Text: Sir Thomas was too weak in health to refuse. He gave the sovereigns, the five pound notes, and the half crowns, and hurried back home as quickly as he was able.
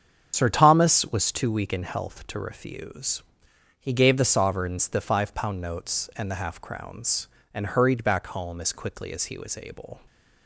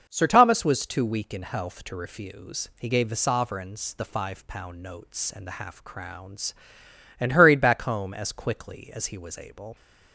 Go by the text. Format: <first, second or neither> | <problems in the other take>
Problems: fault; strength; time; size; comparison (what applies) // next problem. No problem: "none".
second | loses the start of "Sir"; at 0.3 s; 70 ms // starts louder than the rest; strong; until 1.3 s; 7.5 dB